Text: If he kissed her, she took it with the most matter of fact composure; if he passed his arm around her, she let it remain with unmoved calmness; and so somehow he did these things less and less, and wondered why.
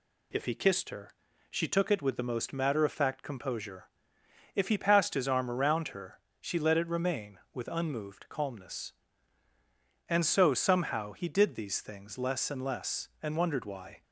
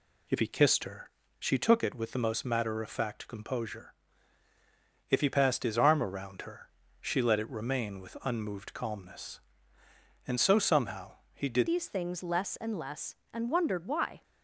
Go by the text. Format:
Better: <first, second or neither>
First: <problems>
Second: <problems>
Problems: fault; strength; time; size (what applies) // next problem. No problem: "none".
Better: first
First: none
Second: pauses between "somehow" and "he"; slight; at 11.1 s; 0.18 s long // changes voice at "these"; from 11.6 s on; 2.6 s long